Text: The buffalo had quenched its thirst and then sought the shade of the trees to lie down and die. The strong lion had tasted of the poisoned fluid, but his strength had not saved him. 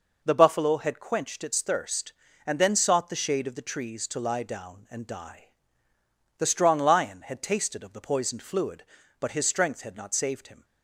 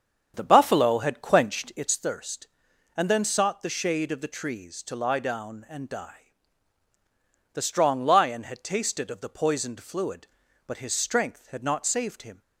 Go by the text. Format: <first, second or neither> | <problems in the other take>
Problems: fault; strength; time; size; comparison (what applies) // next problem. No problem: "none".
first | starts louder than the rest; strong; until 2.0 s; 7.5 dB